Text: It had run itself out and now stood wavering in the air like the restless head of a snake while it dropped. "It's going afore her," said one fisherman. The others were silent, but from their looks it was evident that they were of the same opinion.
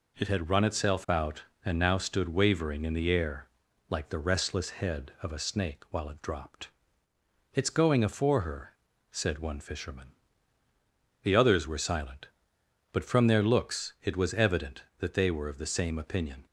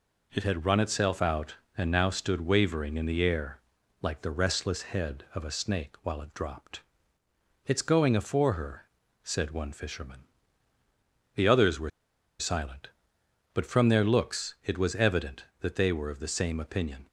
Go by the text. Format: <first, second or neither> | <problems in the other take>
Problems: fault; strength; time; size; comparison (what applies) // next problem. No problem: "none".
first | pauses between "air" and "like"; at 3.5 s; 0.42 s long; also in the first // pauses between "were" and "silent"; noticeable; at 11.8 s; 0.49 s long